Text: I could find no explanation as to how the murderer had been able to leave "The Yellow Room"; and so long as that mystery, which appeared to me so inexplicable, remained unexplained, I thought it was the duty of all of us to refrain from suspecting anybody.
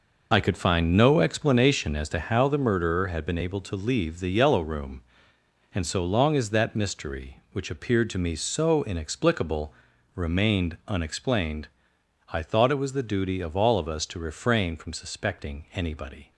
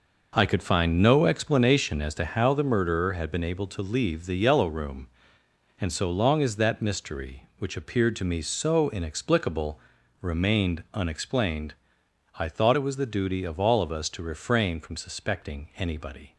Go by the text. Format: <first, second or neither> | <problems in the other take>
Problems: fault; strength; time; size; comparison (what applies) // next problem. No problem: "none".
second | loses the start of "I"; at 0.3 s; 35 ms